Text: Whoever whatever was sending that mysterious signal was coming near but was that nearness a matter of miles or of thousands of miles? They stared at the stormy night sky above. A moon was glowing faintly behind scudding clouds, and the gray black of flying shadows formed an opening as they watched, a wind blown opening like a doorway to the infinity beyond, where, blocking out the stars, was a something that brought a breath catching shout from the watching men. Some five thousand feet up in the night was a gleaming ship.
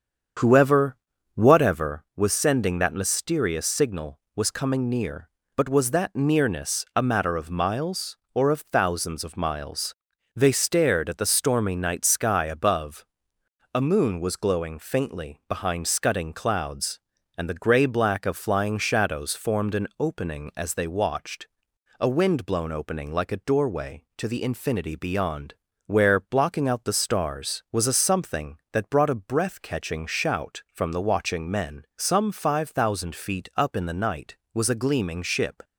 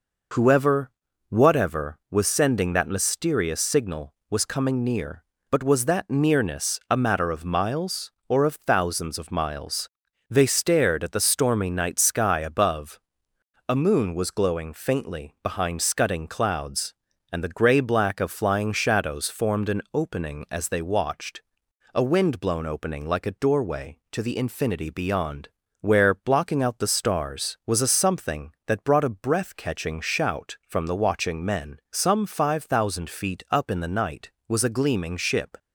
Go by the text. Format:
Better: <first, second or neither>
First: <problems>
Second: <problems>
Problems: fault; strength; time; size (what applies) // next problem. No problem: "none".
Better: second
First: starts louder than the rest; strong; until 2.0 s; 7.5 dB // pauses between "Whoever" and "whatever"; at 0.9 s; 0.38 s long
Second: pauses between "Whoever" and "whatever"; at 0.9 s; 0.38 s long